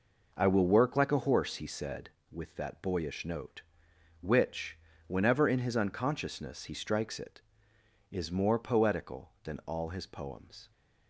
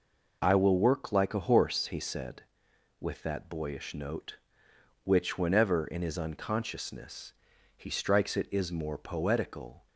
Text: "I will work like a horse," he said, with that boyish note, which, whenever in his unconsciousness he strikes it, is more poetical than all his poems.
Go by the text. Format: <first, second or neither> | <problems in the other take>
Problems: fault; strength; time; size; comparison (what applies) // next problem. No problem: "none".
first | pauses between "unconsciousness" and "he"; at 7.3 s; 0.42 s long // stops before "than all his poems"; at 9.8 s